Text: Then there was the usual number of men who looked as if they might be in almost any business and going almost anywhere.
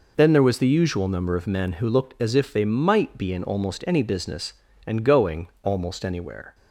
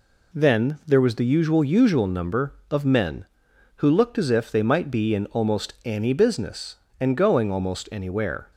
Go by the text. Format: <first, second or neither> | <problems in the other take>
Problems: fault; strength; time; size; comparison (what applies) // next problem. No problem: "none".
first | says "usual" twice; at 1.6 s